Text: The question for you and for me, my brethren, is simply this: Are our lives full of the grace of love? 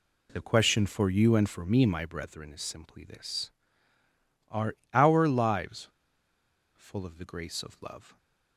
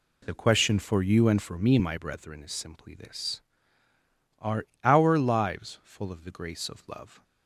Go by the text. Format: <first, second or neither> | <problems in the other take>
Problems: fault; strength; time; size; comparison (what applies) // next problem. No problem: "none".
second | pauses between "Are" and "our"; slight; at 4.7 s; 0.18 s long; slight in the second // pauses between "lives" and "full"; noticeable; at 5.8 s; 0.86 s long